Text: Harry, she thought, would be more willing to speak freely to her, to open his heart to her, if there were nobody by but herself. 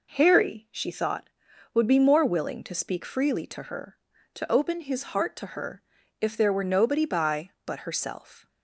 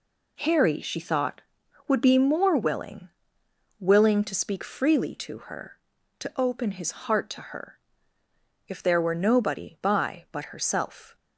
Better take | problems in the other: first | says "willing" twice; at 3.8 s

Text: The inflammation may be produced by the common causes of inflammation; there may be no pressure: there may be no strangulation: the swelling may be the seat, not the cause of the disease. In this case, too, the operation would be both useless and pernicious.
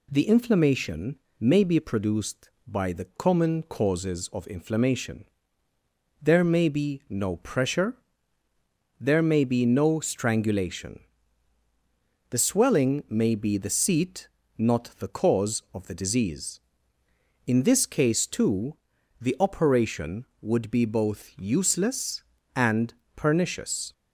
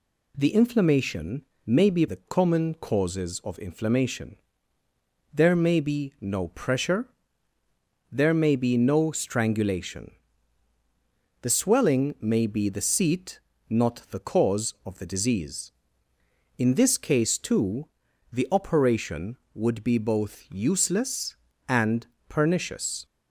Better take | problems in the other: first | pauses between "inflammation" and "may"; slight; at 1.4 s; 0.22 s long; slight in the first // skips "produced by"; at 2.0 s // pauses between "and" and "pernicious"; slight; at 22.0 s; 0.20 s long; slight in the first

